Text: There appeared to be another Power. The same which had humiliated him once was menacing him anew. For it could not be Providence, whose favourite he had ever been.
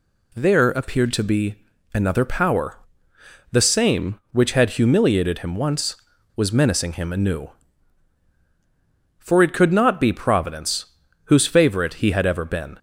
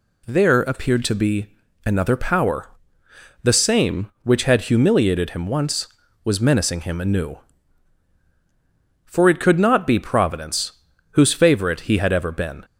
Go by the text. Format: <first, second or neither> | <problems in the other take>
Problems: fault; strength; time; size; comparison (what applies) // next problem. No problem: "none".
neither | pauses between "be" and "another"; the same in both